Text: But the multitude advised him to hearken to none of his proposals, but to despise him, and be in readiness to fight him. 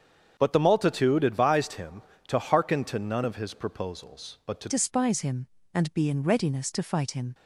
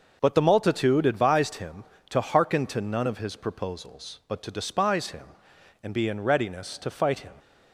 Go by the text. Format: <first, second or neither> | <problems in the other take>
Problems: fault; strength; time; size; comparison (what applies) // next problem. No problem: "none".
second | starts louder than the rest; strong; until 1.3 s; 7 dB // changes voice at "despise"; from 4.6 s on; 2.7 s long